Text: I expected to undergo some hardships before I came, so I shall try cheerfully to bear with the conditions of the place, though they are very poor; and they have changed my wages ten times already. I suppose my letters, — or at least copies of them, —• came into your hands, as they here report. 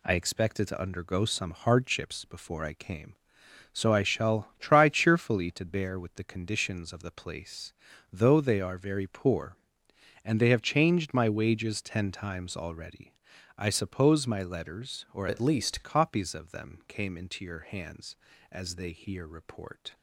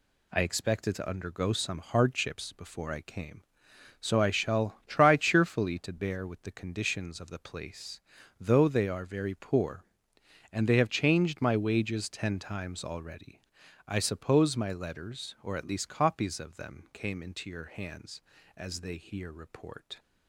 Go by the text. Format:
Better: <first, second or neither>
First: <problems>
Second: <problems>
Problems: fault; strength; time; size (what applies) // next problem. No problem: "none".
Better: second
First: changes voice from "at" to "least"; from 15.2 to 15.8 s; 0.6 s long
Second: none